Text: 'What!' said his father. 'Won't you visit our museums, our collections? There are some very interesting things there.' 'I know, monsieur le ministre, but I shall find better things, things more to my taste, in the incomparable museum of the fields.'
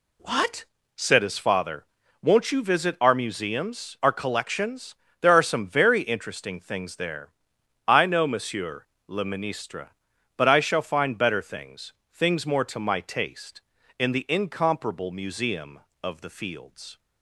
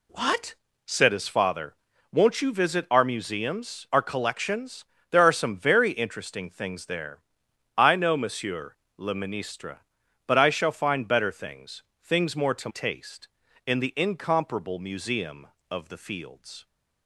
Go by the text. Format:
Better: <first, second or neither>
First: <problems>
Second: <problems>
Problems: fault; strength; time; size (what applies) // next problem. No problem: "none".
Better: first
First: pauses between "monsieur" and "le"; slight; at 8.8 s; 0.22 s long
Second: pauses between "monsieur" and "le"; slight; at 8.7 s; 0.22 s long // skips "my"; at 12.6 s